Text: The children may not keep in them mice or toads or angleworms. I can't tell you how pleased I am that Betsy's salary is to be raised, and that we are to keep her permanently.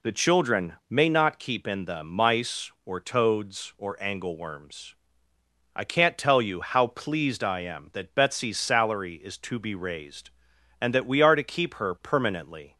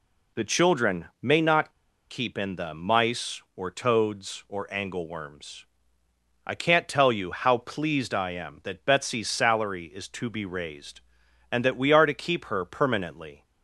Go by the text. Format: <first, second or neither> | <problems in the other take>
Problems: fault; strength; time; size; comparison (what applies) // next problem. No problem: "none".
first | pauses between "children" and "may"; slight; at 1.0 s; 0.16 s long; slight in the first // pauses between "not" and "keep"; at 1.7 s; 0.38 s long